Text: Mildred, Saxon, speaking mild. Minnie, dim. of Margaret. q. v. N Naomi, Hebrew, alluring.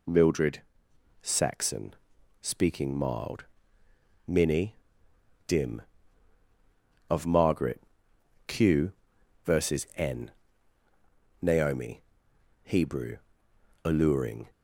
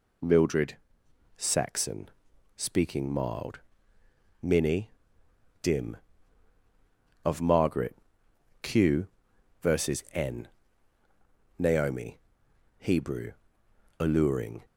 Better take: neither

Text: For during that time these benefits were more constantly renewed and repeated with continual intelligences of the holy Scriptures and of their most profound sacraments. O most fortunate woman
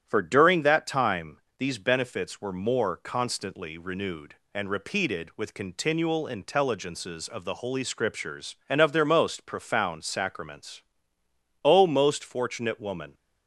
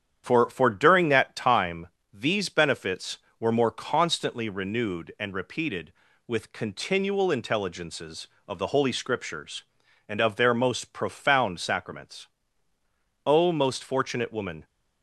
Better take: first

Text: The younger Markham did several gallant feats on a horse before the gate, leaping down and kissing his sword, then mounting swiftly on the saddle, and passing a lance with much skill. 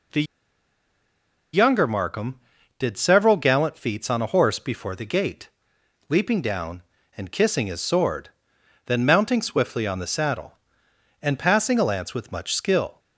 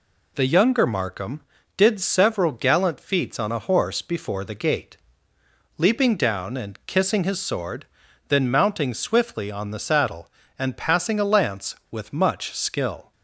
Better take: second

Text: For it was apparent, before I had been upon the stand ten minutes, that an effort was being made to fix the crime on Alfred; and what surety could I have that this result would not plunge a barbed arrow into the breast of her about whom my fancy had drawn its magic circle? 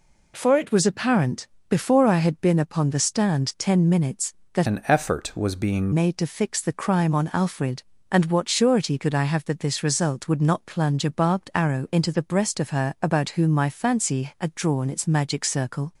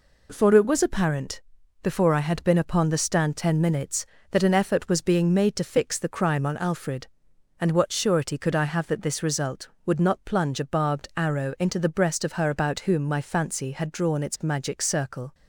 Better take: second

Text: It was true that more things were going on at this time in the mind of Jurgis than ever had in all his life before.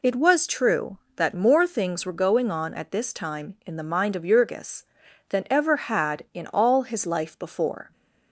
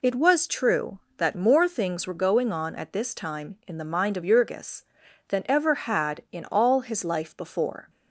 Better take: neither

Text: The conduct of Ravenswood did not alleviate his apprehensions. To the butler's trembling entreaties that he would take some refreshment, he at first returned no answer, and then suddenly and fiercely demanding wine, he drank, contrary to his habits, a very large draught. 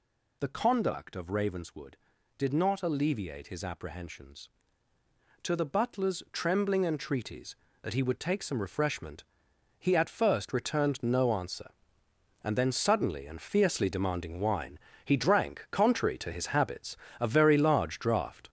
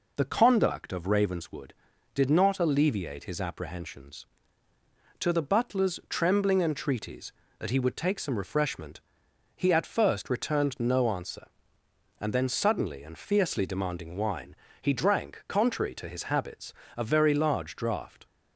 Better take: second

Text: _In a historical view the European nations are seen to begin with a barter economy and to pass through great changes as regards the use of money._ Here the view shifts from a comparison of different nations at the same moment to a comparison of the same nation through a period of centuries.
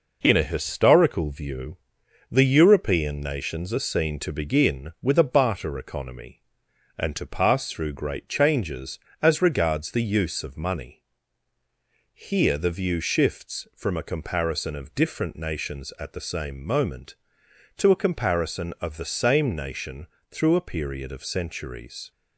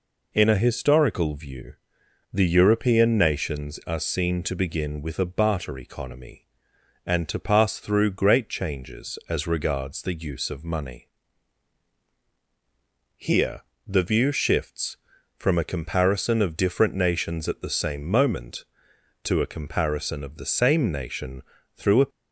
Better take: first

